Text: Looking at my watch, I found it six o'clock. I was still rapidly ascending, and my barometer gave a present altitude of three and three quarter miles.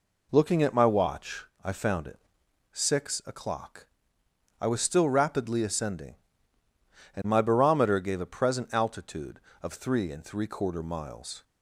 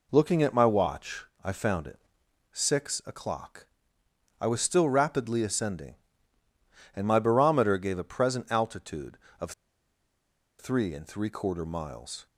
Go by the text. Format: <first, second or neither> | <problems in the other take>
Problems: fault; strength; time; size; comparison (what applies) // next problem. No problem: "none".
first | pauses between "it" and "six"; noticeable; at 1.9 s; 0.52 s long; noticeable in the first // pauses between "of" and "three"; at 9.5 s; 1.0 s long